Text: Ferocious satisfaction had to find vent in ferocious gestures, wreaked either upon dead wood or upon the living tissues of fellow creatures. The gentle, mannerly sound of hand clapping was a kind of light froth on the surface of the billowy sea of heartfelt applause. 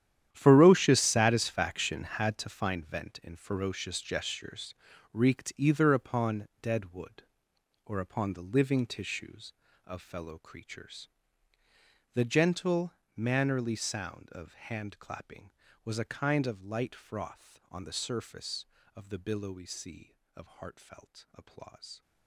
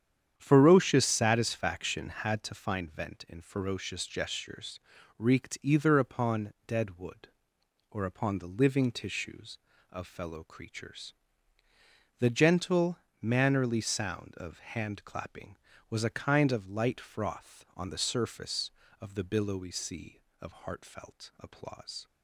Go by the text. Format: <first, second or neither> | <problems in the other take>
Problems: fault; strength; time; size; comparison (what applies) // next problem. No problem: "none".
second | gets quieter; strong; throughout; 15 dB // starts louder than the rest; strong; until 1.3 s; 10.5 dB; strong in the second